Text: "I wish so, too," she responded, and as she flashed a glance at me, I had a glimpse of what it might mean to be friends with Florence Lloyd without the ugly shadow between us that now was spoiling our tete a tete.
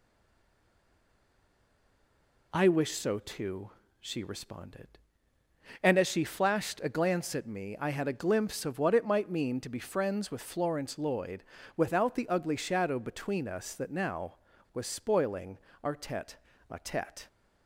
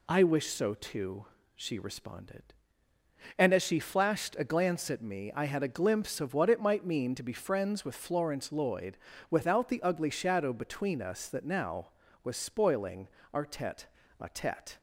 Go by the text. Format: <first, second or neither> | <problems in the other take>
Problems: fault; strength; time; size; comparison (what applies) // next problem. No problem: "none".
second | stays silent before the first word; until 2.5 s; 2.5 s long // pauses between "Lloyd" and "without"; slight; at 11.4 s; 0.34 s long; slight in the second // pauses between "spoiling" and "our"; slight; at 15.5 s; 0.26 s long; slight in the second // pauses between "tete" and "a"; slight; at 16.3 s; 0.32 s long; slight in the second